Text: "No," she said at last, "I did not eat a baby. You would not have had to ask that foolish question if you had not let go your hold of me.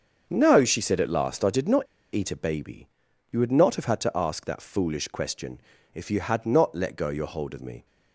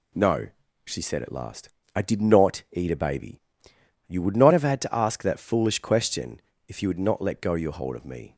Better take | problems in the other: second | starts louder than the rest; until 1.3 s; 6.5 dB // pauses between "not" and "eat"; slight; at 1.8 s; 0.27 s long // pauses between "question" and "if"; slight; at 5.5 s; 0.36 s long; slight in the second

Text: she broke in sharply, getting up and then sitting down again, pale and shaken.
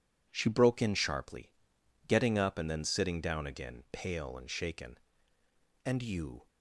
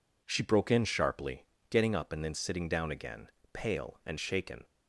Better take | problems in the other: second | goes on to say "And you"; noticeable; from 5.8 s on; 0.62 s long

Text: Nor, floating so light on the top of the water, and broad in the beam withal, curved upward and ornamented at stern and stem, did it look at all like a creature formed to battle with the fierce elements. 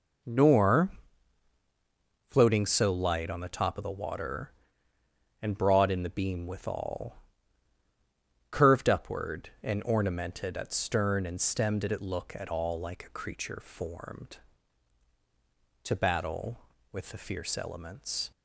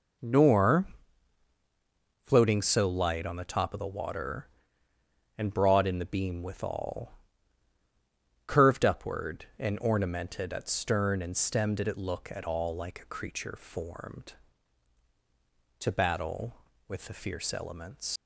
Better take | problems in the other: first | leaves "elements" unfinished; at 18.1 s; 110 ms

